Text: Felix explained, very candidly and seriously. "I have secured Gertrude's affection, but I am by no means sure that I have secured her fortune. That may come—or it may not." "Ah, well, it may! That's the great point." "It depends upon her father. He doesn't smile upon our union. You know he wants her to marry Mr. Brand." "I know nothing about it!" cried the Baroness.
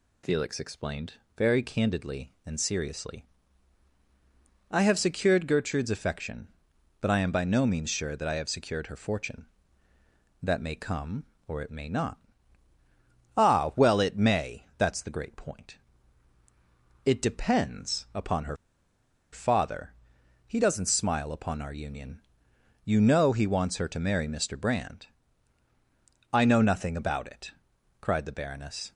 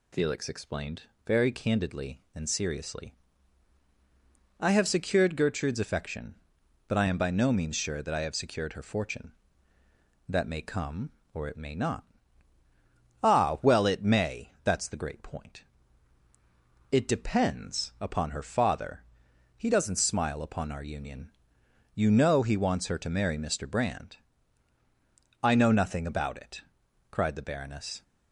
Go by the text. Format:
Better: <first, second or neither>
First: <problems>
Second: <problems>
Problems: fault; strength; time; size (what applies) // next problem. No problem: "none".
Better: second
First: pauses between "her" and "father"; noticeable; at 18.5 s; 0.76 s long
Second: none